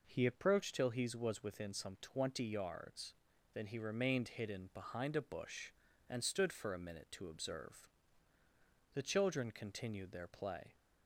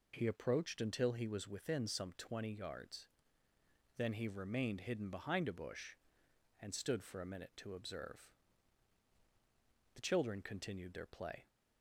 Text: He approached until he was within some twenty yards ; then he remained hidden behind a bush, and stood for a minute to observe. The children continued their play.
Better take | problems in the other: second | says "till" for "until"; at 0.7 s

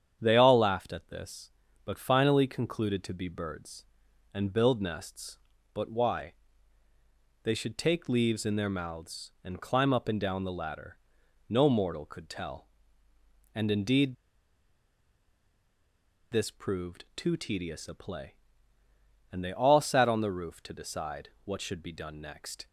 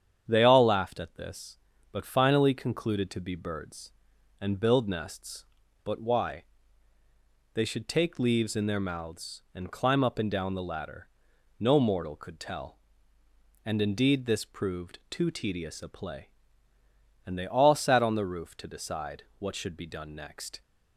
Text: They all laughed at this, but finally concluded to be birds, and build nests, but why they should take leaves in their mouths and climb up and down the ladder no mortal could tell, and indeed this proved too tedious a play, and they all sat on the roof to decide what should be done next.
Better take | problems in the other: second | starts louder than the rest; strong; until 1.2 s; 8.5 dB; strong in the second // pauses between "why" and "they"; at 6.3 s; 1.1 s long; also in the second // pauses between "ladder" and "no"; noticeable; at 10.9 s; 0.52 s long; noticeable in the second // pauses between "indeed" and "this"; strong; at 14.1 s; 2.1 s long // pauses between "decide" and "what"; slight; at 21.2 s; 0.16 s long; slight in the second

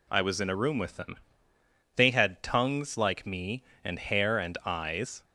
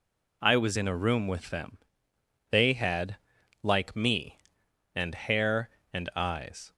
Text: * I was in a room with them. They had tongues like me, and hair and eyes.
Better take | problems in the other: first | skips "tongues"; at 3.3 s

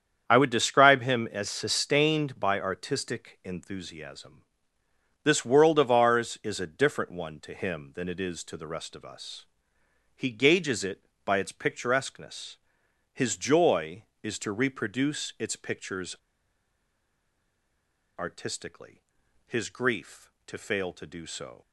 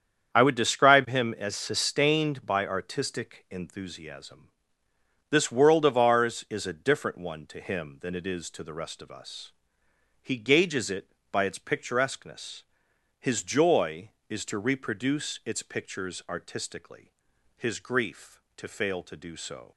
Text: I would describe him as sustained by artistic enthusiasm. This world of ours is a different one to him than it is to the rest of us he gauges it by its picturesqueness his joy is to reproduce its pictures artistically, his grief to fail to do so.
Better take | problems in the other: second | starts louder than the rest; strong; until 1.2 s; 8 dB; strong in the second // pauses between "us" and "he"; noticeable; at 9.4 s; 0.74 s long; noticeable in the second // pauses between "picturesqueness" and "his"; noticeable; at 12.5 s; 0.56 s long; noticeable in the second // pauses between "pictures" and "artistically"; strong; at 16.1 s; 2.0 s long

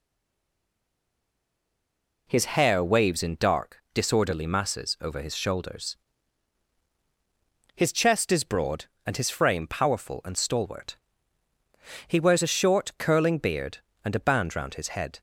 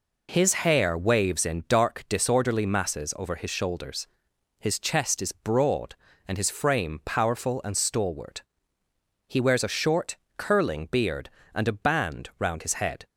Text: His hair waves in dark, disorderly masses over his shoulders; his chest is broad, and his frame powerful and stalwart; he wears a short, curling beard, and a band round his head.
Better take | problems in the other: second | stays silent before the first word; until 2.2 s; 2.2 s long

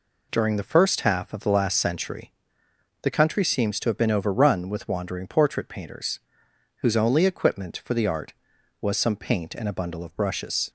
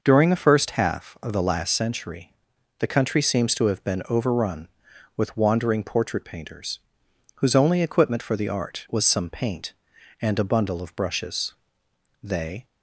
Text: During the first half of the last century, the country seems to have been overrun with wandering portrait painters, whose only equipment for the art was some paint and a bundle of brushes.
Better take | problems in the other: first | goes on to say "They"; slight; from 12.2 s on; 0.42 s long

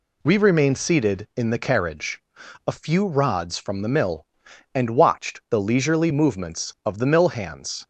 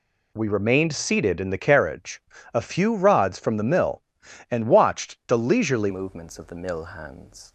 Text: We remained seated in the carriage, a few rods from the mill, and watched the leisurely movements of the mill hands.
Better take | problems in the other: first | changes voice at "movements"; from 5.8 s on; 1.7 s long

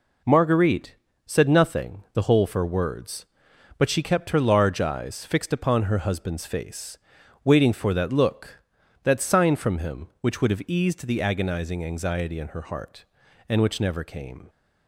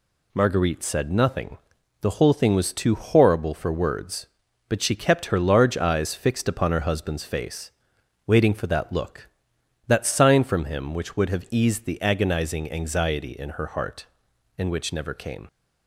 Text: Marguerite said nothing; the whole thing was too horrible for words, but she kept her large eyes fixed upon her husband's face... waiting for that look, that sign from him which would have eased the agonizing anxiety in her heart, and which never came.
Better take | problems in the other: second | pauses between "Marguerite" and "said"; slight; at 0.9 s; 0.30 s long // skips "thing was too horrible"; at 2.4 s

